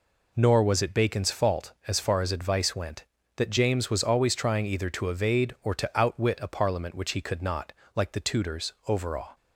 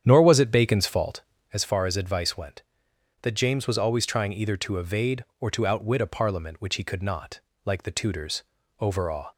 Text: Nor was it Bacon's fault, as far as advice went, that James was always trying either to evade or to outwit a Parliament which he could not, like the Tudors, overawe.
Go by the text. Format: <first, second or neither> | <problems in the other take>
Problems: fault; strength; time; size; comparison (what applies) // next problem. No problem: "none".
first | starts louder than the rest; strong; until 1.6 s; 9 dB